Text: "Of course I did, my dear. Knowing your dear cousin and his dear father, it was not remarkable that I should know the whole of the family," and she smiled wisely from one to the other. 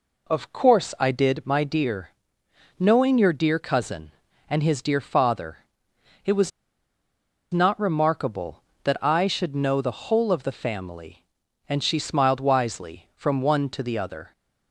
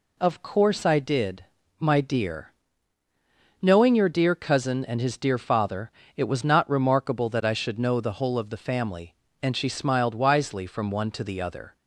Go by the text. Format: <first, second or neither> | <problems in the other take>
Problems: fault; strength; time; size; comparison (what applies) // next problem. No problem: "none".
second | pauses between "was" and "not"; at 6.5 s; 1.0 s long